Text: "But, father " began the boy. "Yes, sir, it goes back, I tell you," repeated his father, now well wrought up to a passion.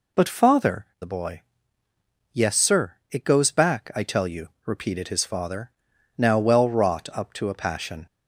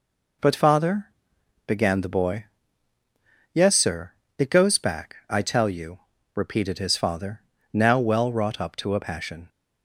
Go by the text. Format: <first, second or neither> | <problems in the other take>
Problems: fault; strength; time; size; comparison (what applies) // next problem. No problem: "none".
second | skips "began"; at 1.0 s